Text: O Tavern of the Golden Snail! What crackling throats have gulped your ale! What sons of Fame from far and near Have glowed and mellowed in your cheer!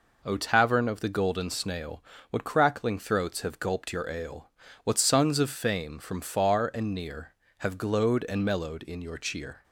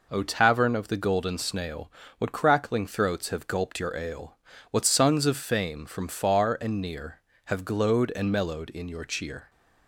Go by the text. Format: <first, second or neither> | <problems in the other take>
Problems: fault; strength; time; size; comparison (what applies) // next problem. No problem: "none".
neither | none